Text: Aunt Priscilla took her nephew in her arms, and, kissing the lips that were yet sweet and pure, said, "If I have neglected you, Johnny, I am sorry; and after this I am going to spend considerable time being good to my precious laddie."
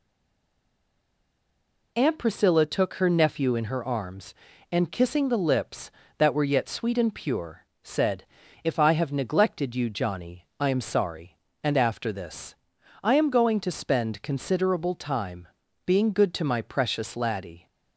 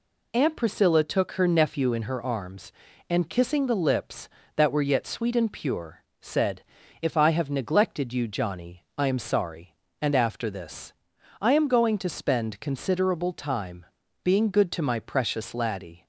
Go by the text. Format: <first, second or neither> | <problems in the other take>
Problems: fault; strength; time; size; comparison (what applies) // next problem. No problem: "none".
second | stays silent before the first word; noticeable; until 1.9 s; 1.9 s long // pauses between "this" and "I"; noticeable; at 12.5 s; 0.48 s long; noticeable in the second // pauses between "time" and "being"; at 15.4 s; 0.38 s long; also in the second